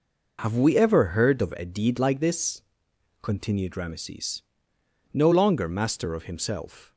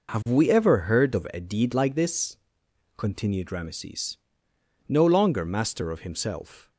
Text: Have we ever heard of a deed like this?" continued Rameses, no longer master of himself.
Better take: neither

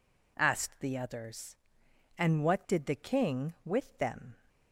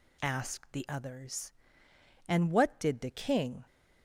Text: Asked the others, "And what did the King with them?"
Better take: first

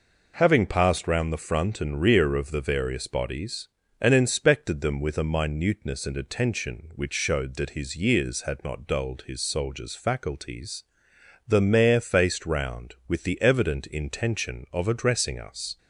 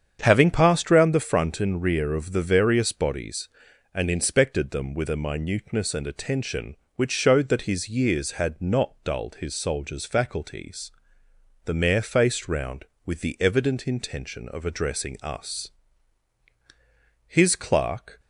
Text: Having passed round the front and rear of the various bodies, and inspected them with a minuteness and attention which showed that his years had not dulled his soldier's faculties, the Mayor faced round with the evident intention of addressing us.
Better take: first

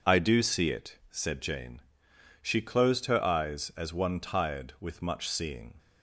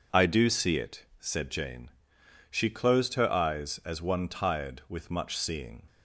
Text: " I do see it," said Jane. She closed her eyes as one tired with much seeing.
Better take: neither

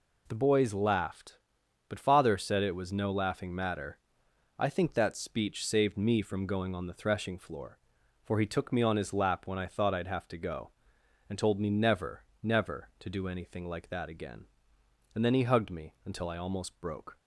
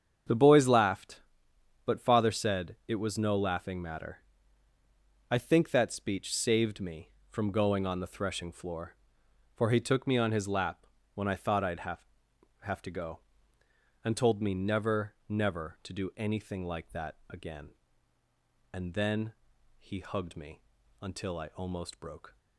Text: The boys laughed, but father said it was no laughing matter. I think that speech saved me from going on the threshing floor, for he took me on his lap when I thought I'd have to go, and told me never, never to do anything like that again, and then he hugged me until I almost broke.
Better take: first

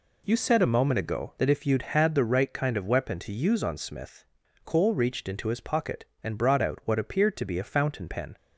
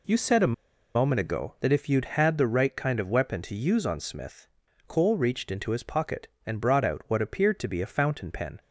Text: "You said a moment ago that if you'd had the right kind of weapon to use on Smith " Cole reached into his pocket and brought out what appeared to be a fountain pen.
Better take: first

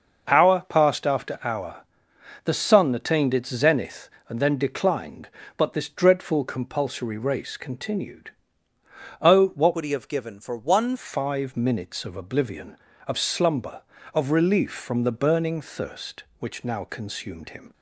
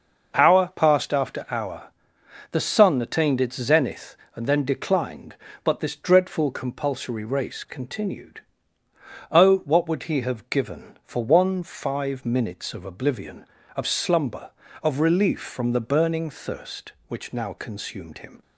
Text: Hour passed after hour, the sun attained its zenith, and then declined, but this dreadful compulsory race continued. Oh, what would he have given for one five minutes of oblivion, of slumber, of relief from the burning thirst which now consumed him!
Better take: second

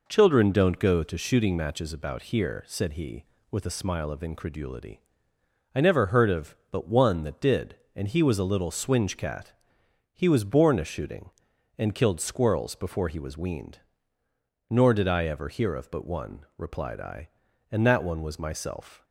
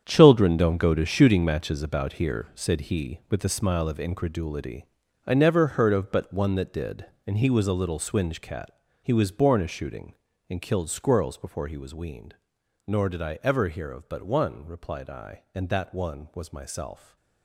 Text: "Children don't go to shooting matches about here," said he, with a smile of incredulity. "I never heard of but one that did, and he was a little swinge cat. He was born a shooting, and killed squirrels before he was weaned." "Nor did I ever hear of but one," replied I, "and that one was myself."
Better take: first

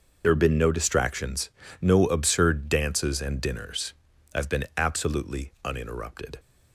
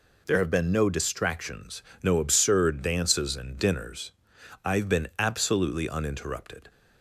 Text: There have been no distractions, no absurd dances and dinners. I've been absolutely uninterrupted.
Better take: second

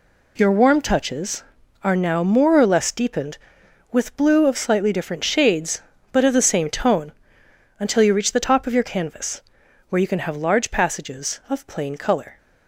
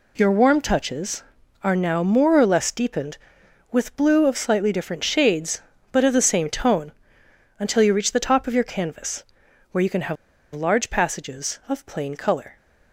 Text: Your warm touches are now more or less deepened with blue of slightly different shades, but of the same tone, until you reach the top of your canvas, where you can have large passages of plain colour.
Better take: first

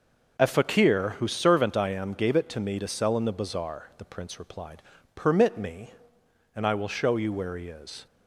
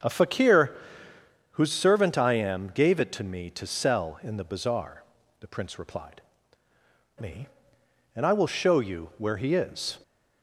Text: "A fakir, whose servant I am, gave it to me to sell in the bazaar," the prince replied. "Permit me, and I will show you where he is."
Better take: first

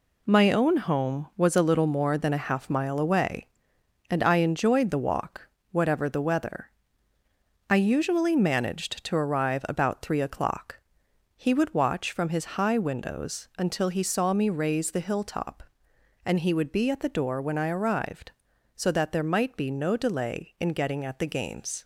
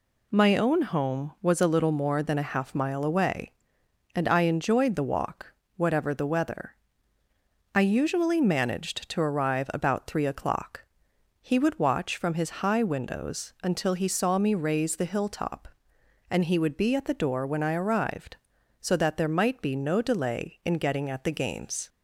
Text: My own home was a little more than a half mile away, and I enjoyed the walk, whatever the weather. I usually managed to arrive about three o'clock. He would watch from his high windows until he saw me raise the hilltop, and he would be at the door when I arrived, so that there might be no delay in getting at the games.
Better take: second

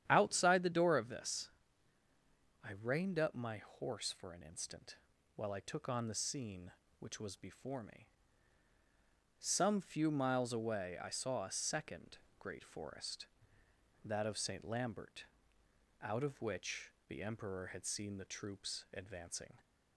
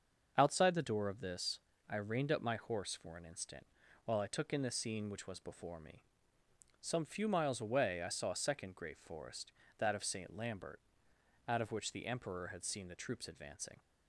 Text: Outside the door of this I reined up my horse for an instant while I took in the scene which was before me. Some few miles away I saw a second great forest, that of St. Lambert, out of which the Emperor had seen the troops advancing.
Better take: second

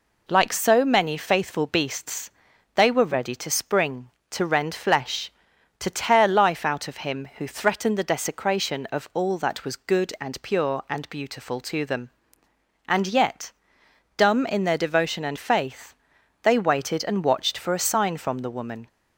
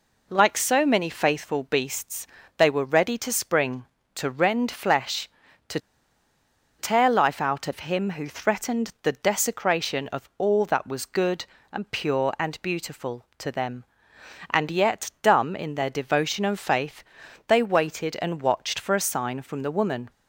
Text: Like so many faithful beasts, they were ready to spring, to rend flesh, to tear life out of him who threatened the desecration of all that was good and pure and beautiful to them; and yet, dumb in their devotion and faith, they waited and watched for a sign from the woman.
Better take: first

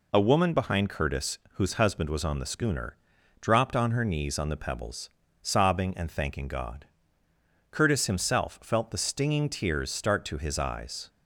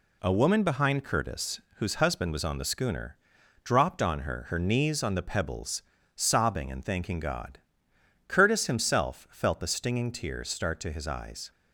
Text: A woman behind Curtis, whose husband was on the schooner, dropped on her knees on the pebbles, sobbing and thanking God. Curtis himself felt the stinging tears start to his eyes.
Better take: first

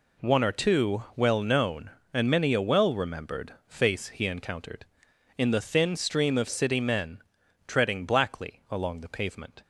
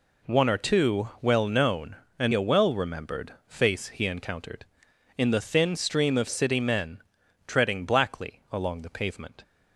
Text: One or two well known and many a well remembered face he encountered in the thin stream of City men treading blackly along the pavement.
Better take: first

